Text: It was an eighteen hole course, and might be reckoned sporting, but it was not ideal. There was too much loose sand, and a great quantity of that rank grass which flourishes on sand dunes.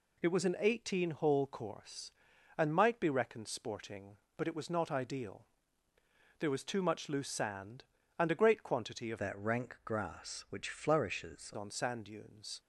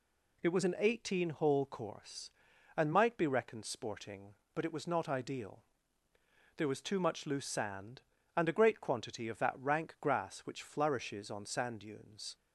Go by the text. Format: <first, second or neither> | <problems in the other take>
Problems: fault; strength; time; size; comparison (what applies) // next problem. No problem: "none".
second | changes voice from "that" to "flourishes"; from 9.1 to 11.5 s; 2.4 s long